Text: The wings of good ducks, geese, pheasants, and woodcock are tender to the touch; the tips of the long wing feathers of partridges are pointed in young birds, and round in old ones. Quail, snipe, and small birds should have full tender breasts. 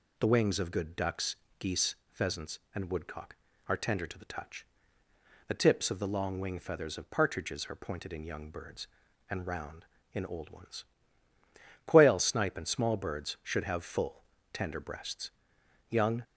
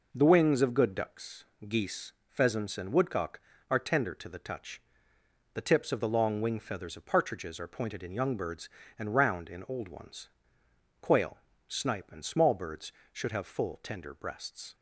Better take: second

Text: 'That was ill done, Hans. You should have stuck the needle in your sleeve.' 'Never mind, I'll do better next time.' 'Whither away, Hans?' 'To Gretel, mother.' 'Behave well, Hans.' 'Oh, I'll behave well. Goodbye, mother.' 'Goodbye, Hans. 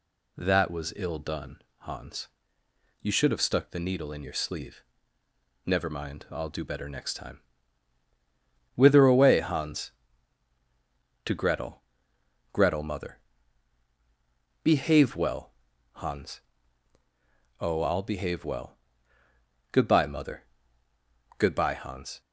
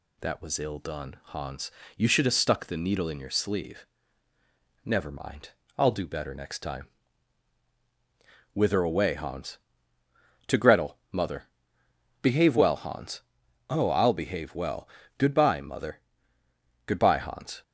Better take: second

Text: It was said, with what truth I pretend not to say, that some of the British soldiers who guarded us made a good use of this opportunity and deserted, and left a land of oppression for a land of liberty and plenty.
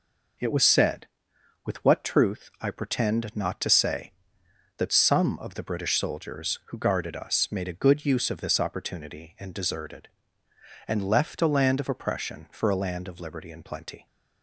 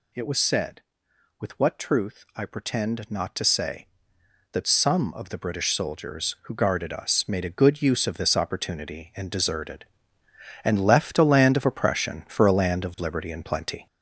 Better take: first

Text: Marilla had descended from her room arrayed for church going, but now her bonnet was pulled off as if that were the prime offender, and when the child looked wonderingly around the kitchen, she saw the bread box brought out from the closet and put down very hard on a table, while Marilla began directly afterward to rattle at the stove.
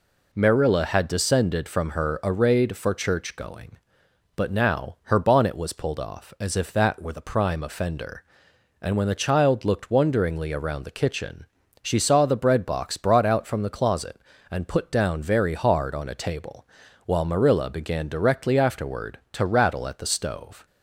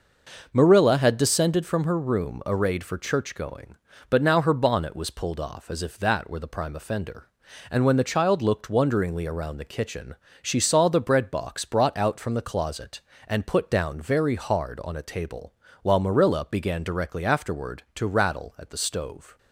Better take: second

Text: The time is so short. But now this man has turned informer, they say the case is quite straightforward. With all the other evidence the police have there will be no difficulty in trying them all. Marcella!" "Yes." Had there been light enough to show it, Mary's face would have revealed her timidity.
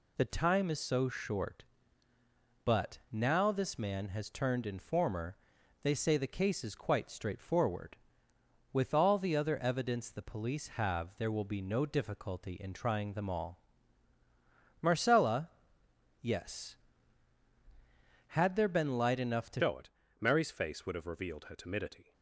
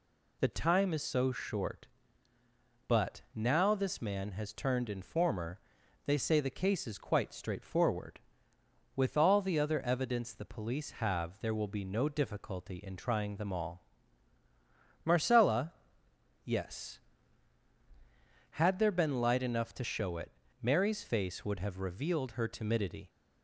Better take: second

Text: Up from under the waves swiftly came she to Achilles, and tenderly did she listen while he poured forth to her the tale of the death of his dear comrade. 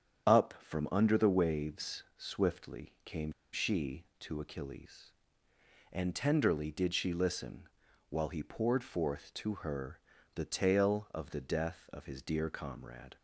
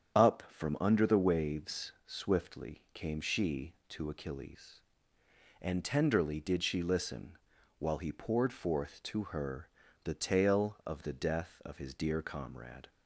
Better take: second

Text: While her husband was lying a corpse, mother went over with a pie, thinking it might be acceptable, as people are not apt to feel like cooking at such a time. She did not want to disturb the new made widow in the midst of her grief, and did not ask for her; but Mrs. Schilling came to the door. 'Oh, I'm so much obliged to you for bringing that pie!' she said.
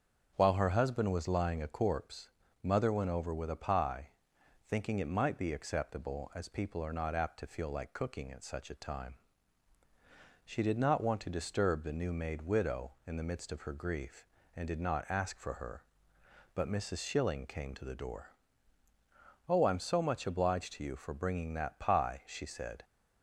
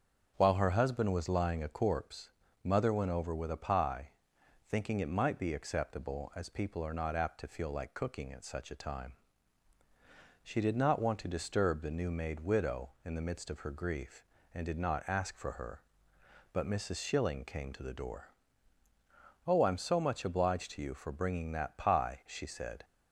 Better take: neither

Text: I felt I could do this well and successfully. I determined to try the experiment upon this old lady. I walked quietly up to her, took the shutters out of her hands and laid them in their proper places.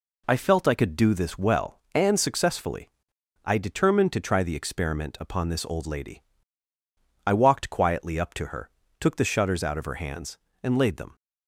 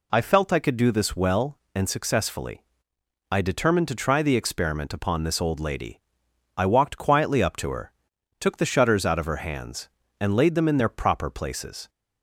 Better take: second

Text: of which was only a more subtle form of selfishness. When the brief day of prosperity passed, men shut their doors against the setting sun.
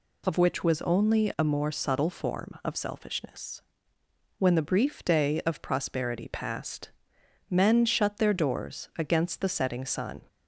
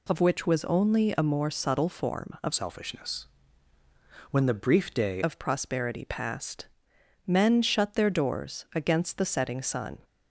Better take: first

